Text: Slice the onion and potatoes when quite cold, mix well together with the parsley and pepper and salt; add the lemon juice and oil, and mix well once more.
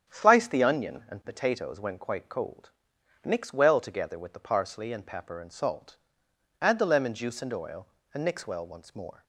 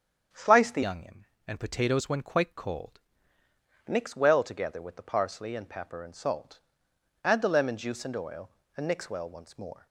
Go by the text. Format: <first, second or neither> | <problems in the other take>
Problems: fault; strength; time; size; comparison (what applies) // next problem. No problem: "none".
first | starts louder than the rest; strong; until 1.5 s; 8 dB; strong in the first // changes voice from "onion" to "cold"; from 0.8 to 2.9 s; 2.1 s long